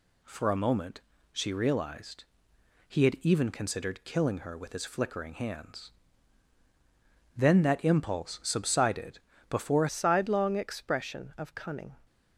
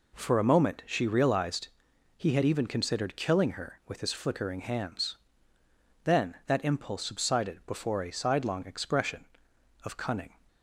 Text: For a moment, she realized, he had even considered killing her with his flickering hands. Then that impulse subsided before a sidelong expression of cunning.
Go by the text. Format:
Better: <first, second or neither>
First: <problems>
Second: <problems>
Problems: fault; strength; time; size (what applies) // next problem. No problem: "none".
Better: second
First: pauses between "subsided" and "before"; slight; at 9.1 s; 0.30 s long // changes voice at "sidelong"; from 9.8 s on; 2.1 s long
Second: none